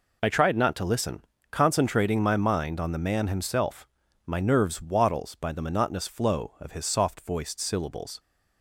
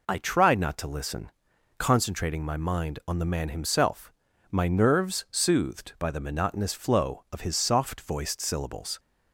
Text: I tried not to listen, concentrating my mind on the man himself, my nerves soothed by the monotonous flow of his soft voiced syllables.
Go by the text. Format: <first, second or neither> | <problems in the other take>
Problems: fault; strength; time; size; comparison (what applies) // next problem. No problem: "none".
second | says "wattles" for "soothed"; at 4.8 s